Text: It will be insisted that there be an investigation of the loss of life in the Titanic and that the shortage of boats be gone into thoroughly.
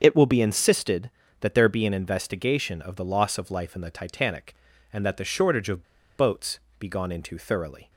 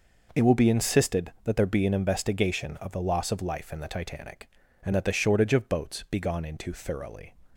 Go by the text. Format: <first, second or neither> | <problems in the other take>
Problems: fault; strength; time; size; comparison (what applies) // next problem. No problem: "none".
second | starts louder than the rest; until 1.0 s; 7 dB // pauses between "of" and "boats"; slight; at 5.8 s; 0.33 s long // pauses between "boats" and "be"; slight; at 6.5 s; 0.20 s long